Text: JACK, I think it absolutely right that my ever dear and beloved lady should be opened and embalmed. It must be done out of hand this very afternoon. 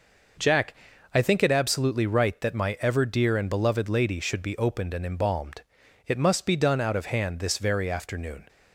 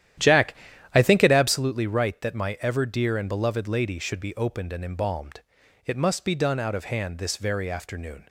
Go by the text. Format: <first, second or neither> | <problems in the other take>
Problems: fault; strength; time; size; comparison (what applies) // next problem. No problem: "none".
first | starts louder than the rest; strong; until 1.6 s; 11.5 dB